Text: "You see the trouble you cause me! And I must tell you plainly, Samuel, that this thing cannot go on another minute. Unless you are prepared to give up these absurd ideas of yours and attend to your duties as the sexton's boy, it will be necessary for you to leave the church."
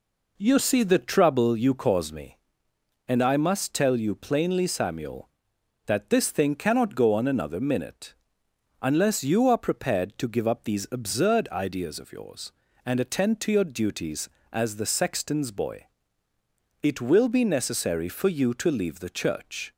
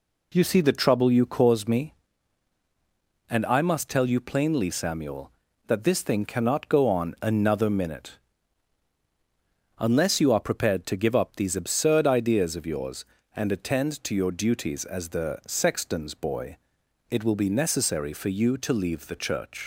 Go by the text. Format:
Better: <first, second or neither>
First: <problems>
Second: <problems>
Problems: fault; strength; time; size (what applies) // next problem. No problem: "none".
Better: first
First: none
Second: leaves "church" unfinished; at 19.6 s; 105 ms